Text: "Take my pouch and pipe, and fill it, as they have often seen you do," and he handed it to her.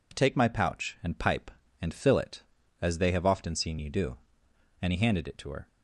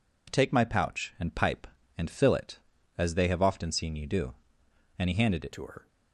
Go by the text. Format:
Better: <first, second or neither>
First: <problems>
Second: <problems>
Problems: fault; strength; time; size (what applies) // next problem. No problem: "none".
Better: first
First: none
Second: changes voice at "to"; from 5.5 s on; 0.3 s long